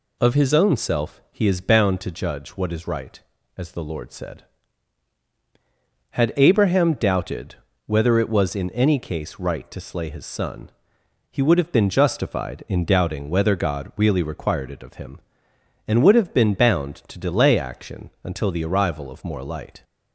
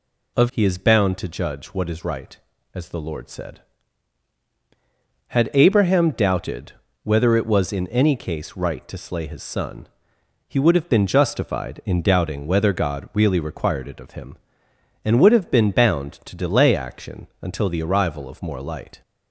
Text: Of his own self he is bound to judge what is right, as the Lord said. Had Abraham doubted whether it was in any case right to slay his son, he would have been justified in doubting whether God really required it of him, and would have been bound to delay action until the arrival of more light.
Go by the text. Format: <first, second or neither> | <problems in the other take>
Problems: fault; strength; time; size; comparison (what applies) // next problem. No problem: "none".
first | skips "his own self"; at 0.4 s // pauses between "doubted" and "whether"; slight; at 6.7 s; 0.32 s long; slight in the first